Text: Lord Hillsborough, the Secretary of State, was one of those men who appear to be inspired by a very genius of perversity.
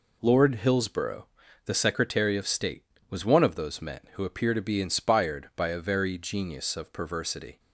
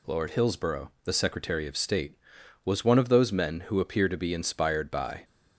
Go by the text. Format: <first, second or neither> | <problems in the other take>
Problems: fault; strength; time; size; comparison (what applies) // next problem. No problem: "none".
first | stops before "a very genius of perversity"; at 5.2 s